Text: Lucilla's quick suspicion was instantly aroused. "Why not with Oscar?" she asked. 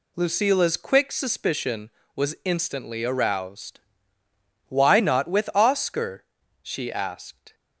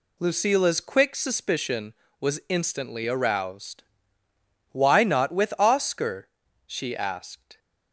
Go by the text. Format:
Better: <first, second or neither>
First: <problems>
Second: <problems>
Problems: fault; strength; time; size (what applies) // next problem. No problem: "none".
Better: neither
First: none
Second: none